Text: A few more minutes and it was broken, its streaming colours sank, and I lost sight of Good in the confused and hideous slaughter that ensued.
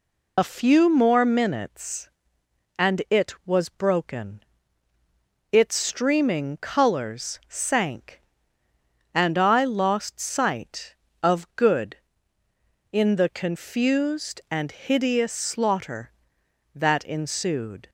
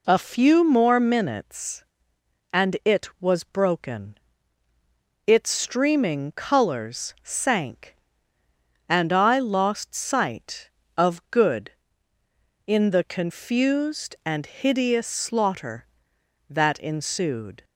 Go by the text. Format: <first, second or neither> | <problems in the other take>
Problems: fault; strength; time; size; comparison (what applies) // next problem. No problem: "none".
second | loses the start of "A"; at 0.3 s; 55 ms